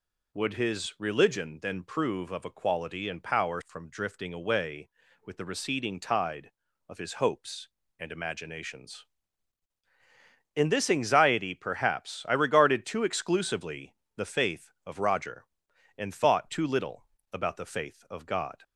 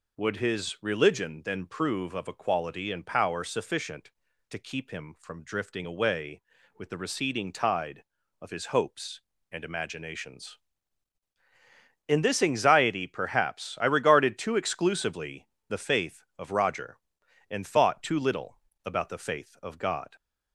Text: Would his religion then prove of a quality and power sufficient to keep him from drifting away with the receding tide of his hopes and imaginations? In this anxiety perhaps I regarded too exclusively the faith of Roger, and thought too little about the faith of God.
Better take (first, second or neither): second